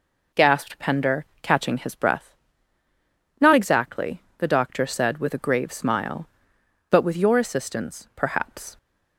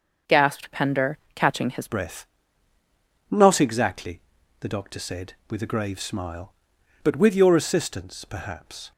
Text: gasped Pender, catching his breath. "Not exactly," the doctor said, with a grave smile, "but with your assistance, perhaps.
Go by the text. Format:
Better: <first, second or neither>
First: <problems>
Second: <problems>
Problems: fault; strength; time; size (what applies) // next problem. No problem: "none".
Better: first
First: none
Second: starts louder than the rest; until 1.4 s; 6.5 dB // changes voice at "breath"; from 1.8 s on; 7.1 s long